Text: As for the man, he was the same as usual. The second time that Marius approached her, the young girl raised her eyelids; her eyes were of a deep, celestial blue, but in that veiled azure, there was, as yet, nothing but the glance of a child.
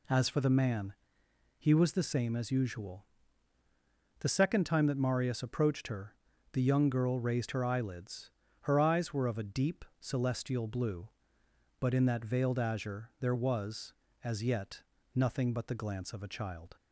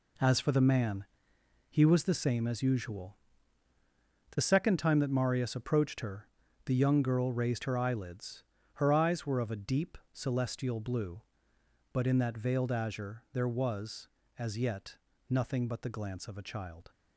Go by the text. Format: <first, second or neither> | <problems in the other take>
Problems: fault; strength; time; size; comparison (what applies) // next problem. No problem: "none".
first | gets quieter; strong; throughout; 9.5 dB